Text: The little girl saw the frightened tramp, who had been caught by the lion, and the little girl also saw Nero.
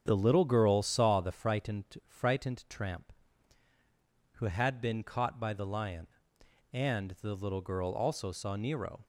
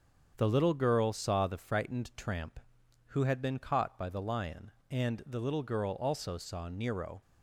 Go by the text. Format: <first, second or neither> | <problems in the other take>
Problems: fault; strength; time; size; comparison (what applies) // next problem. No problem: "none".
second | starts louder than the rest; strong; until 1.0 s; 7.5 dB; strong in the second // says "frightened" twice; at 2.0 s